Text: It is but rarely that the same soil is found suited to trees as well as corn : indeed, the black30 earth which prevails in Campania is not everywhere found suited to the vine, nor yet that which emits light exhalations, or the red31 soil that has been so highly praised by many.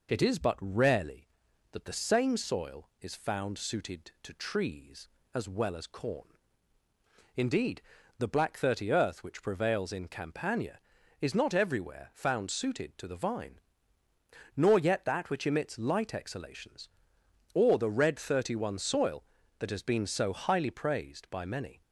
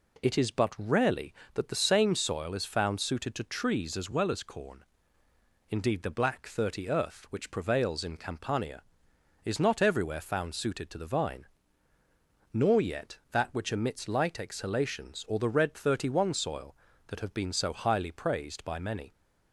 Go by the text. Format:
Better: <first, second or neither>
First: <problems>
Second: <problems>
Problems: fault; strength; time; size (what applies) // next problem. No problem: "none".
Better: first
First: none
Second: says "have" for "has"; at 17.2 s